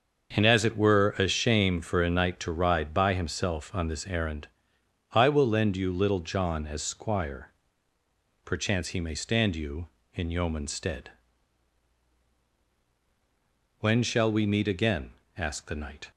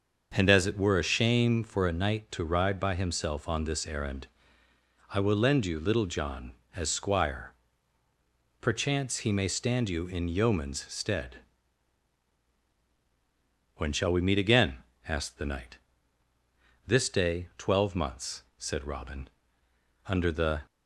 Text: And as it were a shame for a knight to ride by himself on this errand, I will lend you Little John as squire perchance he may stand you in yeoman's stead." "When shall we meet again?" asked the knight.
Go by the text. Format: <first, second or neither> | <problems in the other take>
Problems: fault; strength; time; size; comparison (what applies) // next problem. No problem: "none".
first | starts louder than the rest; until 1.3 s; 6.5 dB; also in the first // pauses between "squire" and "perchance"; at 7.5 s; 1.1 s long; noticeable in the first // goes on to say "This day twelve months said Robin under the"; strong; from 16.8 s on; 3.7 s long